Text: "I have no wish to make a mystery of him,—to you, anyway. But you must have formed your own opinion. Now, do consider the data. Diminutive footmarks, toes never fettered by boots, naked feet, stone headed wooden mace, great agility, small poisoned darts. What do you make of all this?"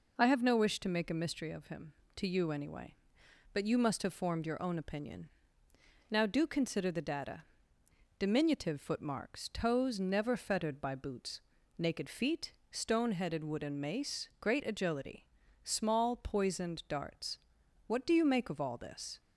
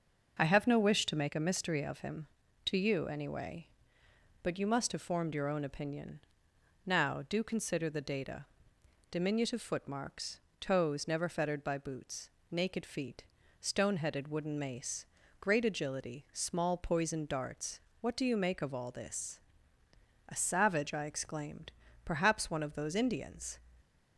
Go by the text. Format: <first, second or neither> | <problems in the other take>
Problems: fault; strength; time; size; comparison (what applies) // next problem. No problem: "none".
first | starts louder than the rest; until 1.3 s; 6 dB // goes on to say "A savage I exclaimed Perhaps one of those Indians"; strong; from 20.2 s on; 3.3 s long